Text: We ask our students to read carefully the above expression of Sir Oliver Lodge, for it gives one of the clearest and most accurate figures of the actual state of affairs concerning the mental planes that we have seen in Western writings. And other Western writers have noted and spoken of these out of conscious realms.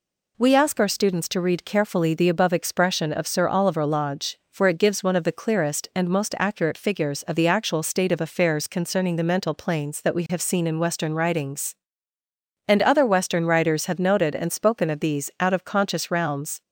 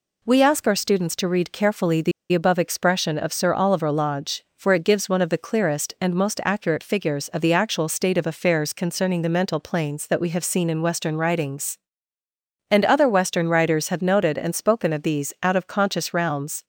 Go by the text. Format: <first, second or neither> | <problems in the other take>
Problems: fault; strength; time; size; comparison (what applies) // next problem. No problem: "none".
first | pauses between "the" and "above"; slight; at 2.1 s; 0.20 s long